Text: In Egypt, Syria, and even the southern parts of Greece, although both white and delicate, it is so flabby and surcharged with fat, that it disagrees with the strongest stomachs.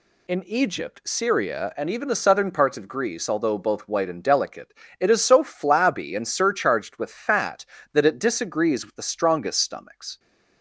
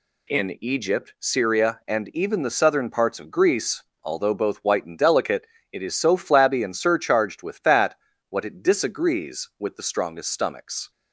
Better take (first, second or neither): first